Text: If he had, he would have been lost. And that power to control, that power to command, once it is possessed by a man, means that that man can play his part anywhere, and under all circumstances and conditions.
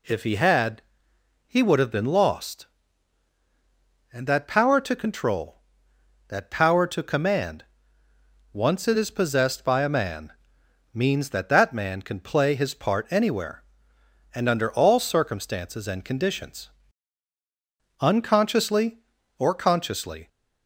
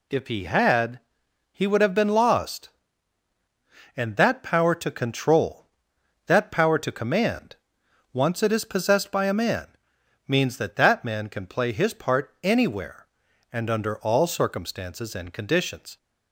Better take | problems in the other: second | goes on to say "Unconsciously or consciously"; strong; from 17.9 s on; 2.2 s long

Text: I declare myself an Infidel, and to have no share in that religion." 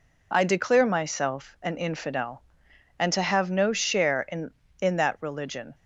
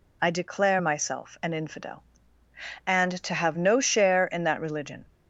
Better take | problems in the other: second | says "in" twice; at 4.7 s

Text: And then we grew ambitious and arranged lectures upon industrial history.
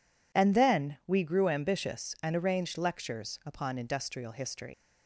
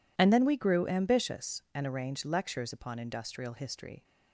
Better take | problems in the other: second | leaves "history" unfinished; at 4.7 s; 120 ms

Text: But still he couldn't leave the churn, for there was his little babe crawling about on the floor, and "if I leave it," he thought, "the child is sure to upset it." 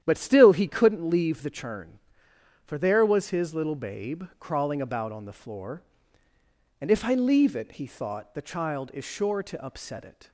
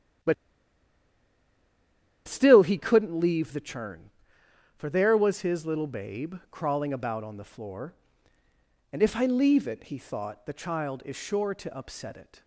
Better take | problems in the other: first | starts louder than the rest; strong; until 3.1 s; 10 dB; strong in the first // pauses between "But" and "still"; strong; at 0.3 s; 1.9 s long

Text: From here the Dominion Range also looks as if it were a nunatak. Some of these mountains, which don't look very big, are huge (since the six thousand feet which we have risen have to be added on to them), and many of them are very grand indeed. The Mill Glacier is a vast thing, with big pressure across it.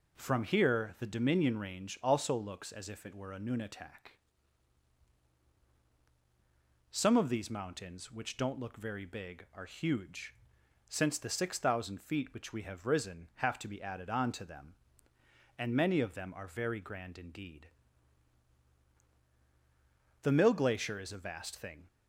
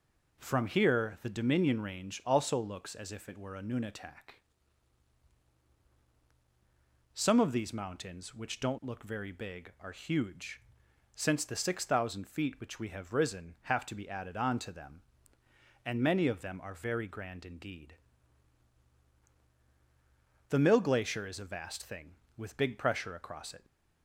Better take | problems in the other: second | stops before "with big pressure across it"; at 21.8 s

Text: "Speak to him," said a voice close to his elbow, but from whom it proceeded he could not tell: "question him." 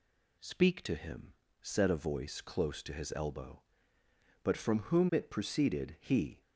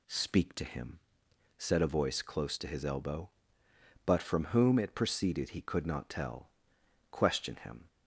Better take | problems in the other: second | stops before "could not tell question him"; at 6.4 s

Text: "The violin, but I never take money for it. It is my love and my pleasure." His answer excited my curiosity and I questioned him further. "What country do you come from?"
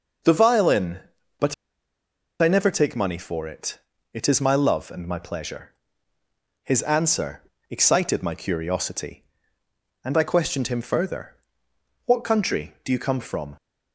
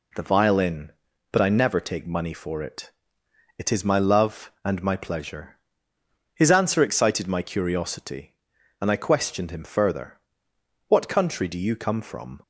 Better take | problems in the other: second | pauses between "but" and "I"; noticeable; at 1.5 s; 0.87 s long // pauses between "answer" and "excited"; slight; at 7.4 s; 0.28 s long

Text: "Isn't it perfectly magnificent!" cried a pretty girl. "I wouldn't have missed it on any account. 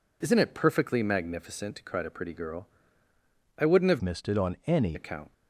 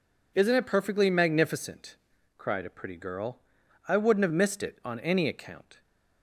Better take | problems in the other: second | changes voice from "missed" to "any"; from 4.0 to 4.9 s; 0.9 s long

